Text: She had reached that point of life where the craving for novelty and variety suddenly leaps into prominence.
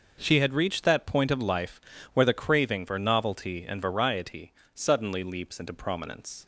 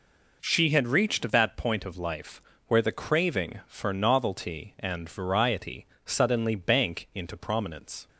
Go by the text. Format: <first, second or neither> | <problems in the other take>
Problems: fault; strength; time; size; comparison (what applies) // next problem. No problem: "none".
first | pauses between "life" and "where"; slight; at 2.4 s; 0.26 s long; slight in the first // pauses between "variety" and "suddenly"; slight; at 5.8 s; 0.20 s long; slight in the first // says "bank" for "leaps"; at 6.5 s